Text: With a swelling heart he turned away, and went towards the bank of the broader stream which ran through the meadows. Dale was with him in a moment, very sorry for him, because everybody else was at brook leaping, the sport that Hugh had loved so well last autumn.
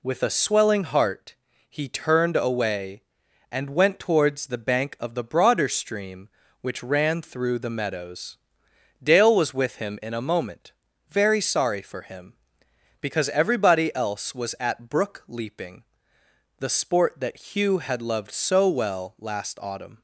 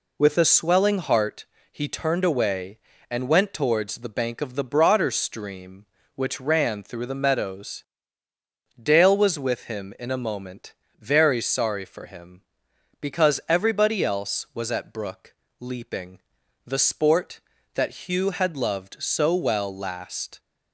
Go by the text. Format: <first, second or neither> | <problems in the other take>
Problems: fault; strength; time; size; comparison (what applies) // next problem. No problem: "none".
first | pauses between "heart" and "he"; slight; at 1.4 s; 0.26 s long; slight in the first // pauses between "brook" and "leaping"; slight; at 15.3 s; 0.24 s long // stops before "autumn"; at 20.3 s